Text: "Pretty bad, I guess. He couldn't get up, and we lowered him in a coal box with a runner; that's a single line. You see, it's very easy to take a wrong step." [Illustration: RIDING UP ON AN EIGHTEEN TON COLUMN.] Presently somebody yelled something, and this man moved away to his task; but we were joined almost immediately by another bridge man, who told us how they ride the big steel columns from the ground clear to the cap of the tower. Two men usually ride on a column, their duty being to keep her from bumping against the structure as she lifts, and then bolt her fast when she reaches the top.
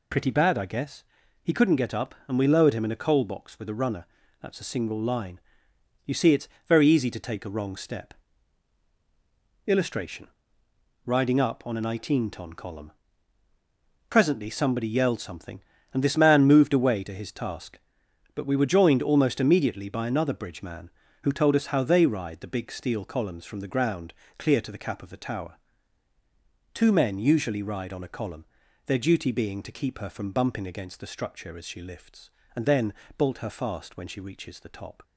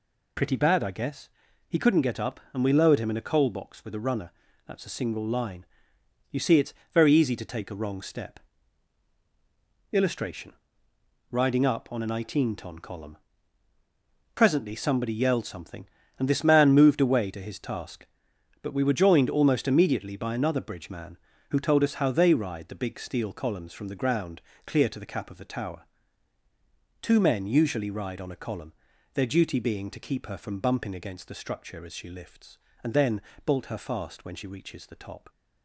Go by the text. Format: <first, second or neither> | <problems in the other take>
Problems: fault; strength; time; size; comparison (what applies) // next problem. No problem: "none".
neither | pauses between "it's" and "very"; slight; the same in both // pauses between "ground" and "clear"; slight; the same in both // pauses between "then" and "bolt"; slight; the same in both